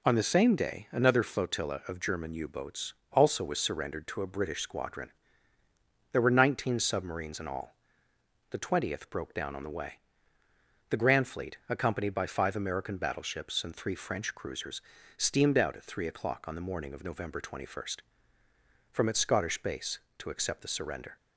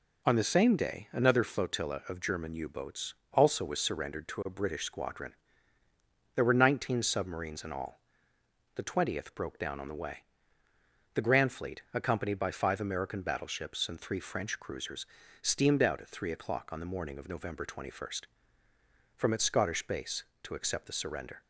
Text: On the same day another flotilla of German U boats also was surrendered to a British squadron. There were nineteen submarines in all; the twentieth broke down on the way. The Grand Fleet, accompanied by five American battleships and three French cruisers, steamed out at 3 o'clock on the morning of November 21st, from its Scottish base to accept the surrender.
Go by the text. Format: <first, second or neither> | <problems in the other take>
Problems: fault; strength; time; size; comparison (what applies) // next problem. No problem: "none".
neither | pauses between "boats" and "also"; slight; the same in both